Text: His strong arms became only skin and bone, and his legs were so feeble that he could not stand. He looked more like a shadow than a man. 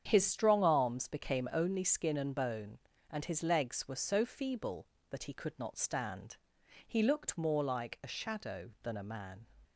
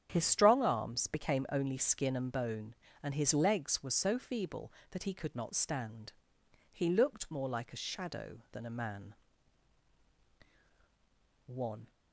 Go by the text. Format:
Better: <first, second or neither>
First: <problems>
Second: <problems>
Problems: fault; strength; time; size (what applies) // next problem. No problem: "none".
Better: first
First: starts louder than the rest; strong; until 1.0 s; 8 dB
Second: starts louder than the rest; strong; until 1.1 s; 8.5 dB // goes on to say "One"; slight; from 11.4 s on; 0.44 s long